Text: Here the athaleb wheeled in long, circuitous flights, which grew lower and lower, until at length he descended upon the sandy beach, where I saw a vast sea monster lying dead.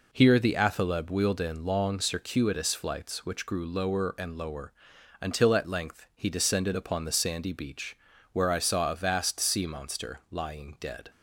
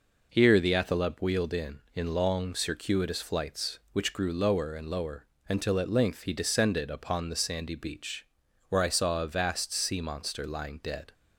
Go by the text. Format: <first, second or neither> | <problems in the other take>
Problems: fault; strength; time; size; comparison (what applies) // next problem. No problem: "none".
first | says "in" twice; at 1.9 s